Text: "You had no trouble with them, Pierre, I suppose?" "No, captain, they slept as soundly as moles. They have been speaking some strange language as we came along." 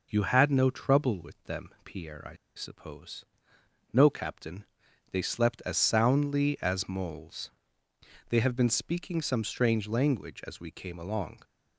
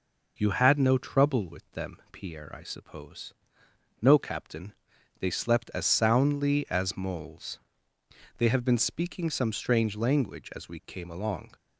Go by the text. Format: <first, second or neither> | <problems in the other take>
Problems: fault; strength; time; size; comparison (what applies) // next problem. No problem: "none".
second | pauses between "I" and "suppose"; slight; at 2.3 s; 0.21 s long